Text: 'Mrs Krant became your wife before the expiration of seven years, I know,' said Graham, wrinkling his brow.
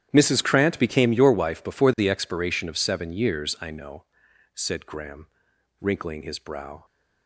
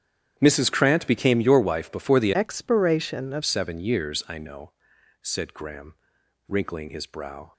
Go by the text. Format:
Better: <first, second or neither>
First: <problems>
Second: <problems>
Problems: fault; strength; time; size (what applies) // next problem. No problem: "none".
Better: first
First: starts louder than the rest; strong; until 1.1 s; 10.5 dB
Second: starts louder than the rest; strong; until 1.3 s; 9.5 dB // changes voice from "expiration" to "of"; from 2.3 to 3.4 s; 1.1 s long